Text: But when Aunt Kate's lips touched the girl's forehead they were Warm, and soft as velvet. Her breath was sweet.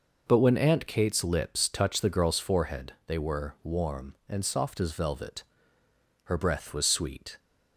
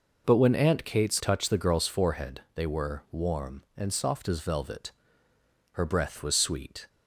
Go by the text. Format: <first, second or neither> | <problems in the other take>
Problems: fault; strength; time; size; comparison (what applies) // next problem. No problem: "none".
first | skips "lips"; at 1.2 s // pauses between "forehead" and "they"; slight; at 2.3 s; 0.16 s long; slight in the first